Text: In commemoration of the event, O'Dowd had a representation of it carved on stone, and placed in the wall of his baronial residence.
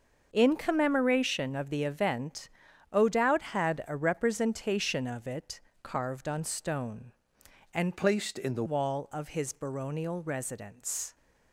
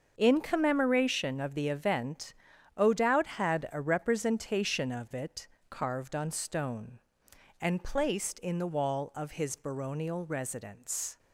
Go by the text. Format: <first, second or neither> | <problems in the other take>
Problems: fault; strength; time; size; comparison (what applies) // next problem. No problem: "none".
second | starts louder than the rest; noticeable; until 1.3 s; 6 dB; also in the second // pauses between "it" and "carved"; slight; at 5.6 s; 0.22 s long; slight in the second // changes voice from "placed" to "the"; from 7.9 to 8.6 s; 0.7 s long